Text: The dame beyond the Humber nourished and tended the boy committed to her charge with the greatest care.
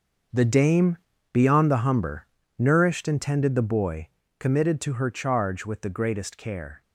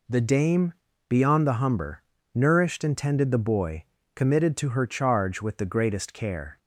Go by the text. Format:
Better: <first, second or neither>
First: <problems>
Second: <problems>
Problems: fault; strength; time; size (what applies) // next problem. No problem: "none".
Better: second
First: gets quieter; strong; throughout; 12.5 dB // pauses between "dame" and "beyond"; slight; at 0.9 s; 0.36 s long // pauses between "Humber" and "nourished"; slight; at 2.2 s; 0.30 s long // pauses between "boy" and "committed"; slight; at 4.0 s; 0.28 s long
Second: pauses between "dame" and "beyond"; slight; at 0.7 s; 0.36 s long // pauses between "Humber" and "nourished"; slight; at 2.0 s; 0.30 s long // pauses between "boy" and "committed"; slight; at 3.8 s; 0.28 s long